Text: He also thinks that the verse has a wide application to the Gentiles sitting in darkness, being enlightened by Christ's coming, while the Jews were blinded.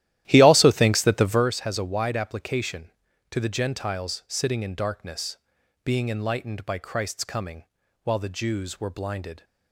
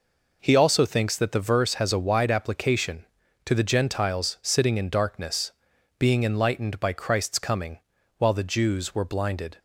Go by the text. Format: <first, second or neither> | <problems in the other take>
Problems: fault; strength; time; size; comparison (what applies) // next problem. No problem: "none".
second | starts louder than the rest; strong; until 1.5 s; 13.5 dB